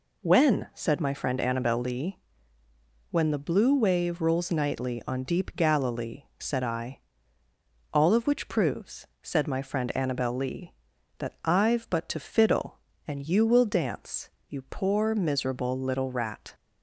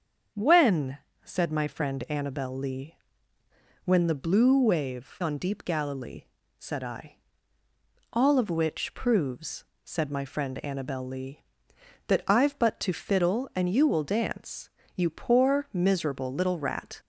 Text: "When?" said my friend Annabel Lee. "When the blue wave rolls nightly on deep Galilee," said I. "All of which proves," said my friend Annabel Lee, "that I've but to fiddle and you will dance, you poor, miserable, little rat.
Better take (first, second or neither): first